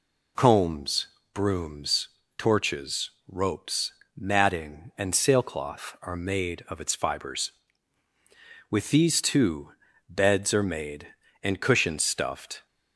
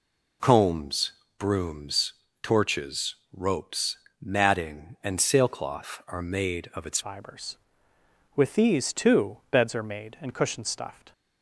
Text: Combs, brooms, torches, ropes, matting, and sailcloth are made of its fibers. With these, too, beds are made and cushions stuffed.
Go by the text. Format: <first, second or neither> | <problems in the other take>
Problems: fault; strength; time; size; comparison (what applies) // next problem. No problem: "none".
first | changes voice at "fibers"; from 7.0 s on; 4.1 s long